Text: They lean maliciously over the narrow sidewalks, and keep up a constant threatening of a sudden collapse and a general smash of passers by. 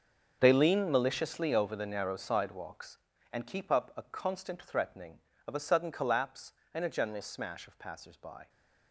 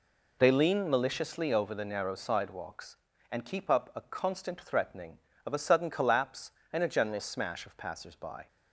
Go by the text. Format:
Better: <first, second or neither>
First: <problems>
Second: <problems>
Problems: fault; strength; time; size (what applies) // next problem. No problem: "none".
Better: second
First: gets quieter; strong; throughout; 14.5 dB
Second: none